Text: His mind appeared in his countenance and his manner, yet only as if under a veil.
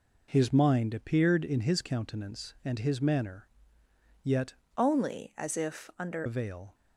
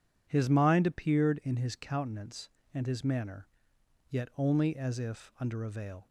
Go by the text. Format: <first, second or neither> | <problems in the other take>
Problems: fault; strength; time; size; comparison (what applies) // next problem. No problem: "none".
second | changes voice from "only" to "under"; from 4.7 to 6.2 s; 1.5 s long